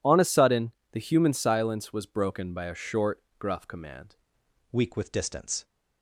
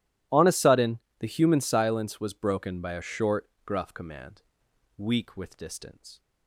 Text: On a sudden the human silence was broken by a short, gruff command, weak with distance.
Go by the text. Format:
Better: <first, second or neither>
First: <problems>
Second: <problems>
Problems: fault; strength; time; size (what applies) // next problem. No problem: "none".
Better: second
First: pauses between "sudden" and "the"; slight; at 0.7 s; 0.22 s long // changes voice at "weak"; from 4.7 s on; 0.9 s long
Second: pauses between "sudden" and "the"; slight; at 0.9 s; 0.22 s long